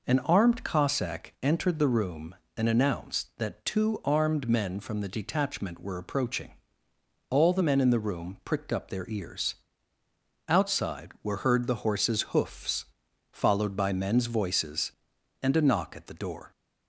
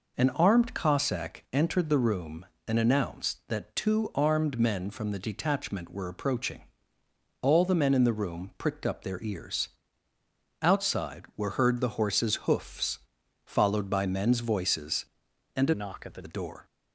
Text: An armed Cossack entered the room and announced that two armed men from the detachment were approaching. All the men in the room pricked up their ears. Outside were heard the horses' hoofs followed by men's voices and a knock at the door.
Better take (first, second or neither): first